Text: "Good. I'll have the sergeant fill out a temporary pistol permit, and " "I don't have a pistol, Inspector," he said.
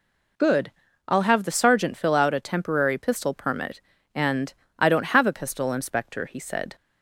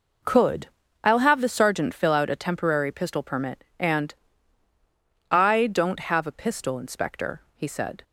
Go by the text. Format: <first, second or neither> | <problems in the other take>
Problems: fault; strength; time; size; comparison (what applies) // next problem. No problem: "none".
first | says "Could" for "Good"; at 0.2 s